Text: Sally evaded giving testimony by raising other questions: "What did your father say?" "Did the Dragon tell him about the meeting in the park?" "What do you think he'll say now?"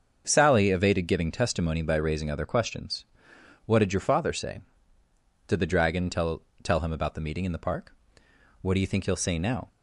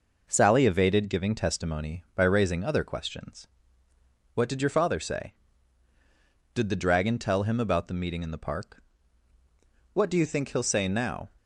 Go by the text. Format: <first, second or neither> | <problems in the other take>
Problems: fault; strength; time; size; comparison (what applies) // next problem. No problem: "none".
second | starts louder than the rest; until 1.2 s; 6.5 dB // says "tell" twice; at 6.6 s